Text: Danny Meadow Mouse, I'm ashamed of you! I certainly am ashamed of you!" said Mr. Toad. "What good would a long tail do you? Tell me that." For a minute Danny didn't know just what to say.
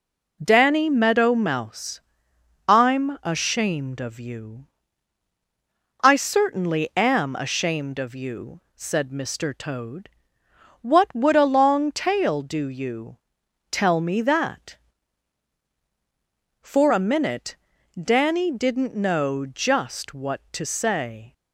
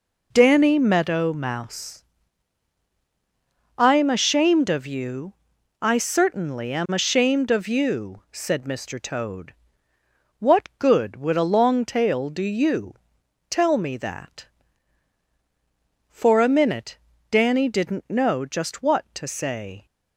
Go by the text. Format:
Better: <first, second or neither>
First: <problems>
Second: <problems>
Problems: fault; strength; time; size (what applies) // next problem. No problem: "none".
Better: second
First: skips "good"; at 11.1 s // pauses between "minute" and "Danny"; at 17.5 s; 0.44 s long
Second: pauses between "minute" and "Danny"; slight; at 16.9 s; 0.32 s long